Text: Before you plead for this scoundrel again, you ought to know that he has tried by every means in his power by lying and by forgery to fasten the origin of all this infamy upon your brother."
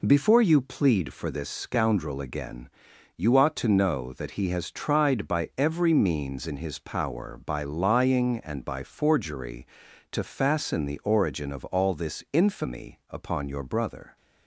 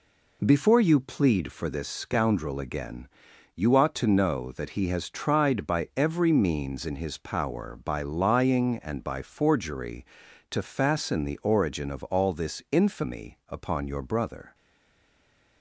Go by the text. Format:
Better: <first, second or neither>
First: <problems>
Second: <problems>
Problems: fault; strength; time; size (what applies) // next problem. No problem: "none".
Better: first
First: none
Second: stays silent after the last word; from 14.5 s on; 1.1 s long